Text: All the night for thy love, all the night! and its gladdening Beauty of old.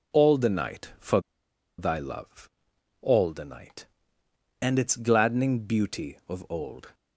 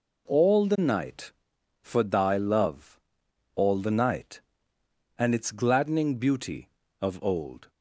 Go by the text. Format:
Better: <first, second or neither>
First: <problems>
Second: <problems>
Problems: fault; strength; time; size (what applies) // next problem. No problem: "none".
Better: second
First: pauses between "for" and "thy"; noticeable; at 1.1 s; 0.58 s long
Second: none